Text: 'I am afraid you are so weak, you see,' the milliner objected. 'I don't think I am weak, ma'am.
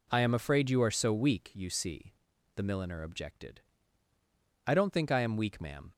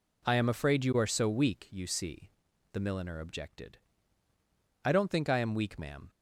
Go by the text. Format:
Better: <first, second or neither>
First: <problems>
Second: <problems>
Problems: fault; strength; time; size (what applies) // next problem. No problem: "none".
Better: neither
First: none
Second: none